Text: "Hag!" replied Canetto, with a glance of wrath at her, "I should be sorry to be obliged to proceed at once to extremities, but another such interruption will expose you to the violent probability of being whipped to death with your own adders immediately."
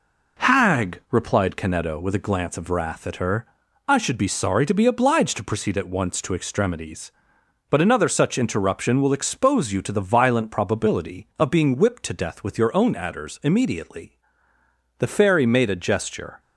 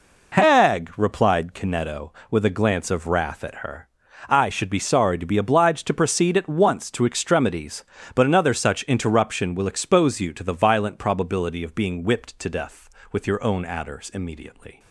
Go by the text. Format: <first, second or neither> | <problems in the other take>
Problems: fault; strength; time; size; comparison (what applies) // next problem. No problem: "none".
second | goes on to say "The fairy made a gesture"; from 14.9 s on; 1.4 s long